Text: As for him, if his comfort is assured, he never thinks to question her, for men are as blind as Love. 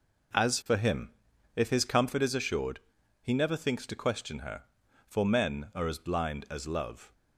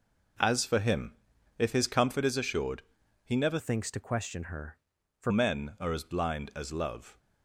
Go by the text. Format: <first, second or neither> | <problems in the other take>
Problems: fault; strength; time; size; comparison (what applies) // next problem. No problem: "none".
first | changes voice from "thinks" to "for"; from 3.5 to 5.3 s; 1.8 s long